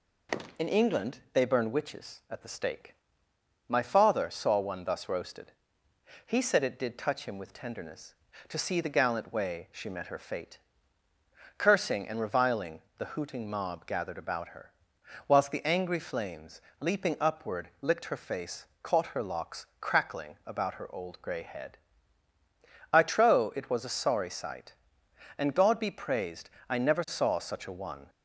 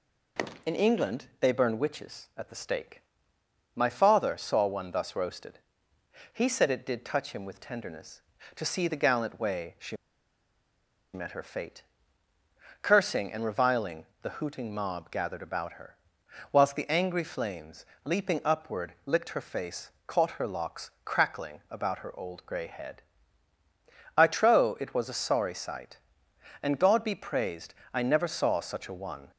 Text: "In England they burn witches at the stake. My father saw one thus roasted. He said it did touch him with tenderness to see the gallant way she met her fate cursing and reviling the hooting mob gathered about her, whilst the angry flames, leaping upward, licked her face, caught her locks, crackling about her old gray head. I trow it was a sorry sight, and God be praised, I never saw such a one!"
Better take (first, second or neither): first